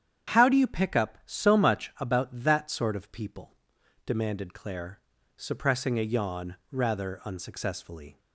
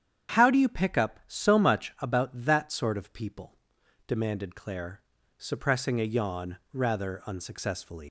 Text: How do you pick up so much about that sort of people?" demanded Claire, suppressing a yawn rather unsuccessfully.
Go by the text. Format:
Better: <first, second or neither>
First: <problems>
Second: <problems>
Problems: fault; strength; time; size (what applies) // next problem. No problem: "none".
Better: first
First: starts louder than the rest; strong; until 1.4 s; 9 dB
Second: starts louder than the rest; strong; until 1.4 s; 9 dB // leaves "unsuccessfully" unfinished; at 8.0 s; 115 ms